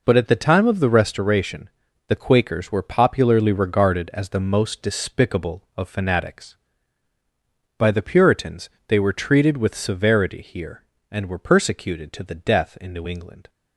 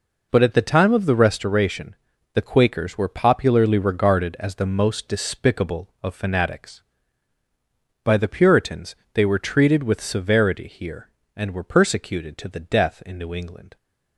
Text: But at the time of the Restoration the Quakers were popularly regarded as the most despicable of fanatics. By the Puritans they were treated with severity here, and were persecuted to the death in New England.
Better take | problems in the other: neither | pauses between "Restoration" and "the"; the same in both // pauses between "Puritans" and "they"; slight; the same in both

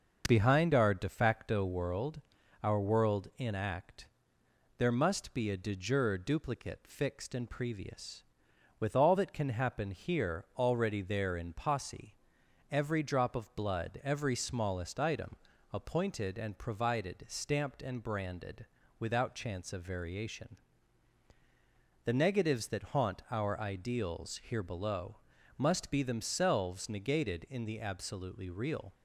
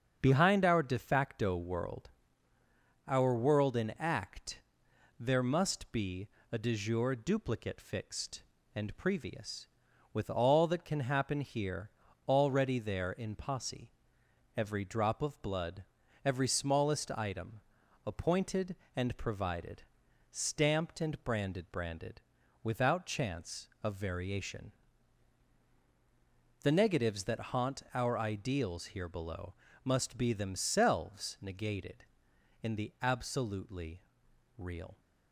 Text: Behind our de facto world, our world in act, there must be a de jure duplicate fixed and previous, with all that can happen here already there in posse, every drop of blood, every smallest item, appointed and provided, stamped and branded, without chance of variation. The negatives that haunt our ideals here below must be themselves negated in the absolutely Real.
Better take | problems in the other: first | starts louder than the rest; until 1.2 s; 7 dB; noticeable in the first // pauses between "be" and "a"; slight; at 6.2 s; 0.24 s long // pauses between "here" and "already"; at 11.8 s; 0.38 s long // says "branded" twice; at 21.7 s // pauses between "below" and "must"; slight; at 29.5 s; 0.32 s long; also in the first // pauses between "absolutely" and "Real"; noticeable; at 34.0 s; 0.56 s long

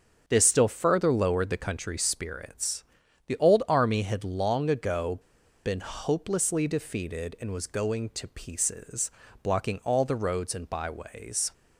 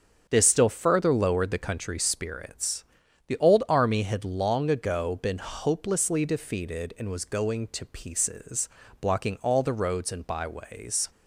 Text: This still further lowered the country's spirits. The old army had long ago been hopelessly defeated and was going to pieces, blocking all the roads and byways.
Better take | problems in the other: second | starts louder than the rest; strong; until 1.2 s; 7 dB; strong in the second // pauses between "ago" and "been"; noticeable; at 5.1 s; 0.46 s long

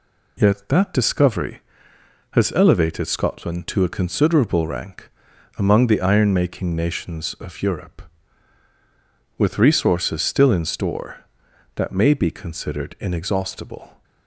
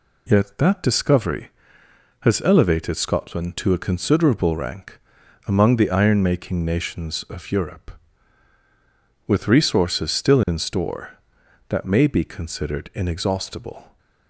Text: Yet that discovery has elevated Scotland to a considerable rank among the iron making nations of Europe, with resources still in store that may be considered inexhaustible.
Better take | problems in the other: neither | pauses between "rank" and "among"; noticeable; the same in both

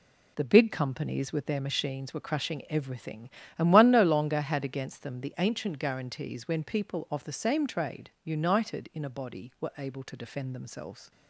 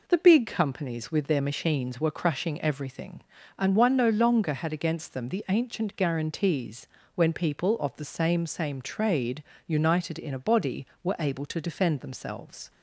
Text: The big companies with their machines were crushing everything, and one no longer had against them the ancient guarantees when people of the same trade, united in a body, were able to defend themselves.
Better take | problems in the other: first | pauses between "guarantees" and "when"; slight; at 6.8 s; 0.28 s long // says "same" twice; at 8.4 s

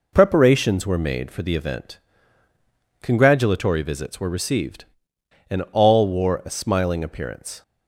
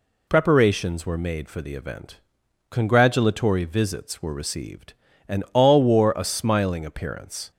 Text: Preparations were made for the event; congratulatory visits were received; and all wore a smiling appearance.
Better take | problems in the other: neither | none

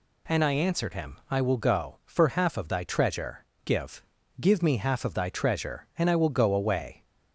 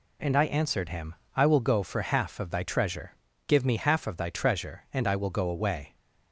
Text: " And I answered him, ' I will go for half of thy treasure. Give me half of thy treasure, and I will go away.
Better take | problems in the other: second | says "Give" twice; at 4.4 s

